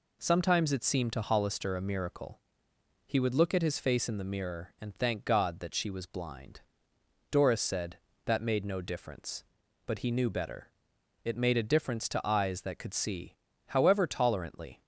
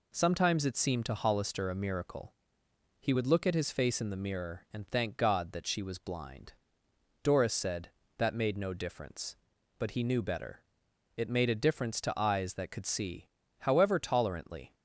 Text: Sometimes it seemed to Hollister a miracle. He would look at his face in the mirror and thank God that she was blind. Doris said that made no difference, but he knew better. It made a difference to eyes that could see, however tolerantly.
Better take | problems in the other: neither | none

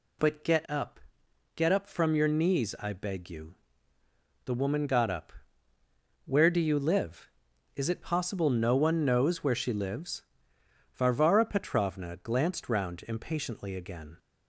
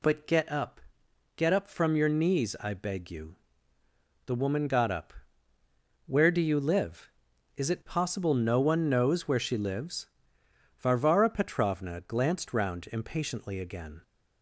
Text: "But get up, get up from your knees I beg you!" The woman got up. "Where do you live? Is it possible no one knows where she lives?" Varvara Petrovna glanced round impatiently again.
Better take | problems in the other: neither | none

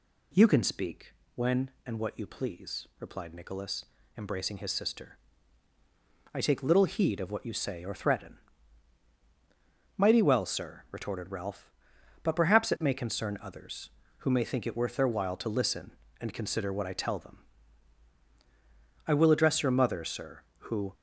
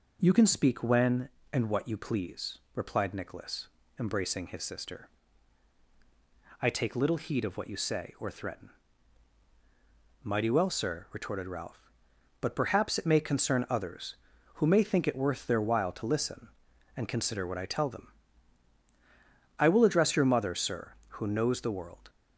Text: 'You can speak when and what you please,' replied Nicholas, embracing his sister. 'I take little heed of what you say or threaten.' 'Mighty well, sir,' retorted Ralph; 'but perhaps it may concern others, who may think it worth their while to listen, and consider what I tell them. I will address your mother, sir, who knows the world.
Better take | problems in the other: second | pauses between "speak" and "when"; slight; at 1.1 s; 0.22 s long // stops before "knows the world"; at 20.9 s

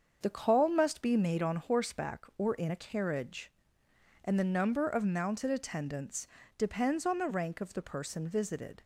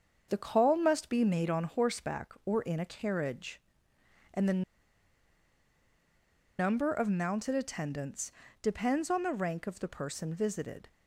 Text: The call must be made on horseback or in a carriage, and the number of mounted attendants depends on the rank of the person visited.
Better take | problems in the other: first | starts louder than the rest; until 1.3 s; 7 dB; also in the first // pauses between "the" and "number"; strong; at 4.6 s; 1.9 s long // pauses between "attendants" and "depends"; slight; at 8.3 s; 0.30 s long; slight in the first

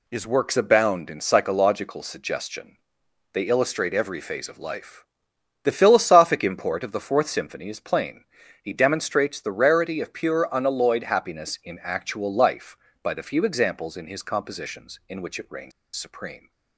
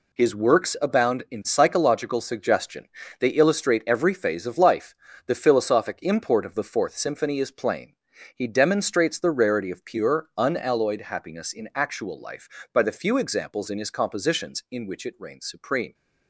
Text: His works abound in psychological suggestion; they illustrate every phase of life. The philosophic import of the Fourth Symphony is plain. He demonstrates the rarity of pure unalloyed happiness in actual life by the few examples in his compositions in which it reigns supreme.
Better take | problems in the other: second | pauses between "reigns" and "supreme"; slight; at 15.7 s; 0.24 s long

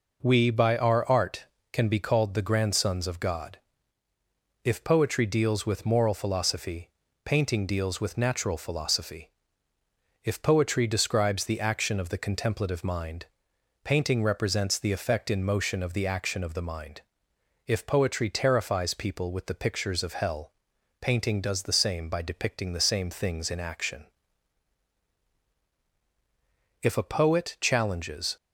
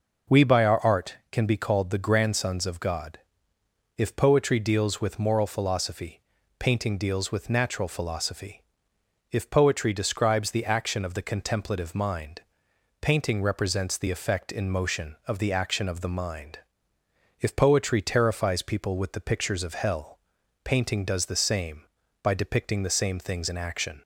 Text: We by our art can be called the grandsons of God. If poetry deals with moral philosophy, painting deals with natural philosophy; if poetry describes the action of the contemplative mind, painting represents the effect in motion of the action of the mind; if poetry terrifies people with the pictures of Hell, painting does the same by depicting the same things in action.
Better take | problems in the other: second | goes on to say "If a poet challenges"; from 26.8 s on; 1.5 s long

